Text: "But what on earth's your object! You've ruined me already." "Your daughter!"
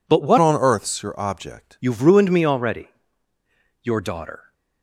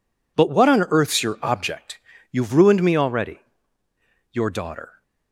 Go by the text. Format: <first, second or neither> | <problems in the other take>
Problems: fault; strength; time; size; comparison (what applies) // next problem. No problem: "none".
second | changes voice from "on" to "object"; from 0.3 to 1.7 s; 1.4 s long